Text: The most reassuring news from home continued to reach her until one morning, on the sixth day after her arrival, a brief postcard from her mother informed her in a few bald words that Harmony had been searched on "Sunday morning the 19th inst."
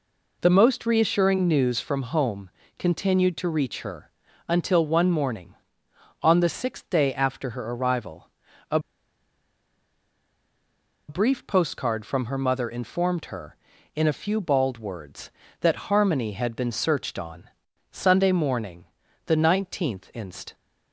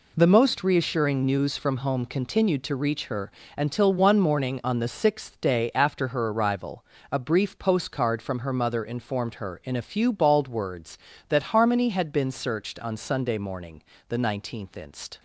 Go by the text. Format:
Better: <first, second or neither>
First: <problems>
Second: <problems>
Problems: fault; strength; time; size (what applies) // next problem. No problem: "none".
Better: second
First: pauses between "home" and "continued"; slight; at 2.4 s; 0.28 s long // pauses between "her" and "until"; slight; at 4.1 s; 0.36 s long // pauses between "a" and "brief"; strong; at 8.7 s; 2.2 s long // pauses between "on" and "Sunday"; at 17.4 s; 0.42 s long // pauses between "morning" and "the"; at 18.8 s; 0.42 s long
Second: pauses between "her" and "until"; slight; at 3.3 s; 0.26 s long // pauses between "morning" and "the"; slight; at 13.8 s; 0.26 s long